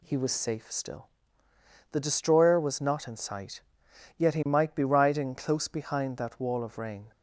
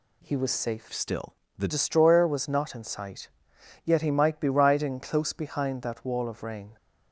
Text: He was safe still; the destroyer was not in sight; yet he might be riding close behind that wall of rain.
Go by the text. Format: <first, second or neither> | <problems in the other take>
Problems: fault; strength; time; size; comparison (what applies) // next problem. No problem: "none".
first | changes voice from "still" to "the"; from 0.9 to 1.6 s; 0.7 s long